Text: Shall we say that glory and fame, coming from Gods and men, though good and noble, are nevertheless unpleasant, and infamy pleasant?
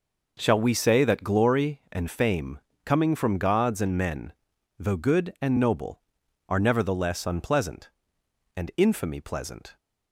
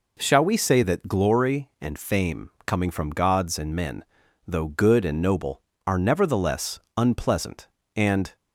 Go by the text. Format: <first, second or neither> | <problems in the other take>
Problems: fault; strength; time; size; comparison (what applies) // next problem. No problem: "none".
first | pauses between "nevertheless" and "unpleasant"; slight; at 6.7 s; 0.18 s long // stops before "infamy pleasant"; at 8.3 s